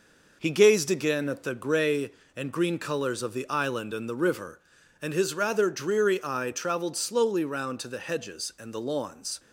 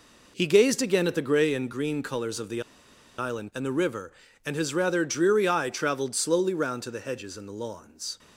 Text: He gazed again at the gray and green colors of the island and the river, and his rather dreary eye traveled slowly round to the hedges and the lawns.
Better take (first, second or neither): first